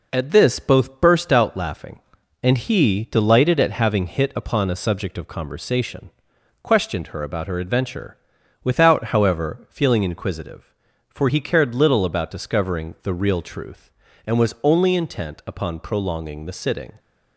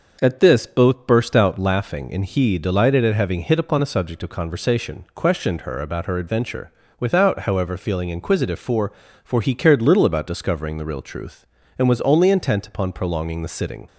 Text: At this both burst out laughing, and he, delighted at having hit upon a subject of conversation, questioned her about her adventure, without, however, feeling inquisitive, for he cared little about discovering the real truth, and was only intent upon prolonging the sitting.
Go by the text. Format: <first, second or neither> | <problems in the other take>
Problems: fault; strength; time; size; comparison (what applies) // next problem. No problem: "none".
first | says "for" twice; at 9.2 s